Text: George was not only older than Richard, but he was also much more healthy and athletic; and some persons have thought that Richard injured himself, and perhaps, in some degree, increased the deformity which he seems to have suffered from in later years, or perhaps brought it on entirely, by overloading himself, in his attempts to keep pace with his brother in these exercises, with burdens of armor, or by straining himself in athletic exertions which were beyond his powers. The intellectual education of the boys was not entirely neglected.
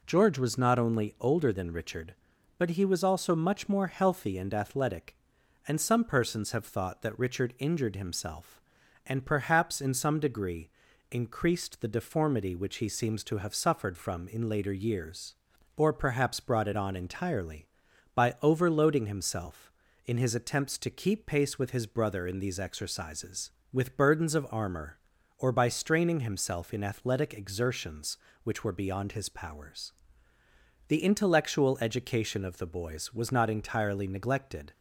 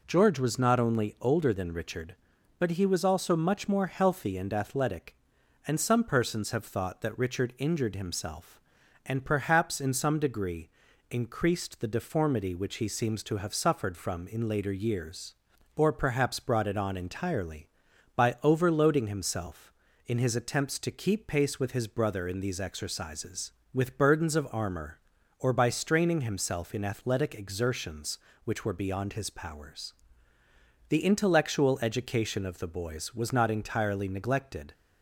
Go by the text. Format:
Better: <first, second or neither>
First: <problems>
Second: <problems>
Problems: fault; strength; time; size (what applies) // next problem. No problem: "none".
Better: neither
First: none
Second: none